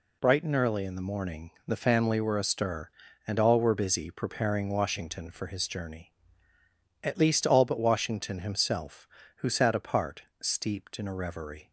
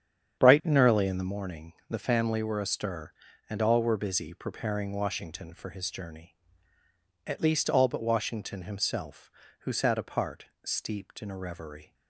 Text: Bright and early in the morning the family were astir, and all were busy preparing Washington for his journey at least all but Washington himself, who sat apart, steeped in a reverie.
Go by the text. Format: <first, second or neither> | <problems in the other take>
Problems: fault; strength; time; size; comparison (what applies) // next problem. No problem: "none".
first | starts louder than the rest; strong; until 1.4 s; 8.5 dB